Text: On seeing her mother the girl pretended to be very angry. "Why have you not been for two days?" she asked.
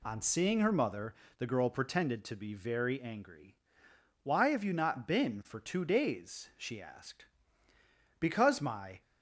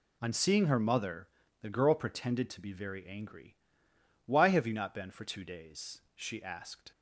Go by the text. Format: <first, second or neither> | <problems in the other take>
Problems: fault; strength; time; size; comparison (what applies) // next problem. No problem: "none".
second | pauses between "mother" and "the"; slight; at 1.1 s; 0.24 s long; slight in the second // goes on to say "Because my"; noticeable; from 8.2 s on; 0.80 s long